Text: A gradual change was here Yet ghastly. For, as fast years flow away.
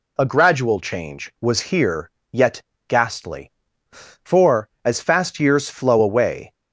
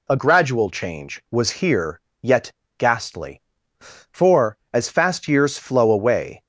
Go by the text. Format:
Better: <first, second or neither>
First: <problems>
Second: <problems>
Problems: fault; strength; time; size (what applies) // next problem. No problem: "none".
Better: neither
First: pauses between "here" and "Yet"; slight; at 2.1 s; 0.22 s long // pauses between "Yet" and "ghastly"; slight; at 2.6 s; 0.26 s long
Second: pauses between "here" and "Yet"; slight; at 2.0 s; 0.22 s long // pauses between "Yet" and "ghastly"; slight; at 2.5 s; 0.26 s long